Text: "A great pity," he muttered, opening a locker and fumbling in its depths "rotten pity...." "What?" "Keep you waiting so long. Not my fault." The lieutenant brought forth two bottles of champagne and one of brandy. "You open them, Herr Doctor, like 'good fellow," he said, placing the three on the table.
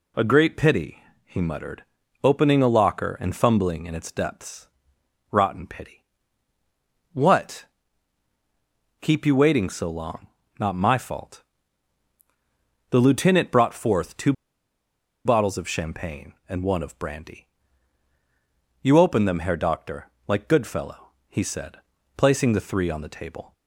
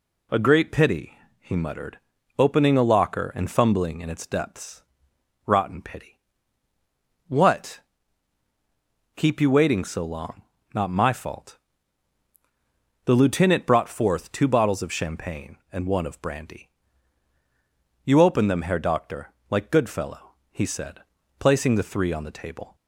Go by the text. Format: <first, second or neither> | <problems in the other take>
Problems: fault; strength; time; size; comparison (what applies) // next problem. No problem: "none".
second | pauses between "depths" and "rotten"; noticeable; at 4.6 s; 0.64 s long; noticeable in the second // pauses between "two" and "bottles"; noticeable; at 14.3 s; 0.93 s long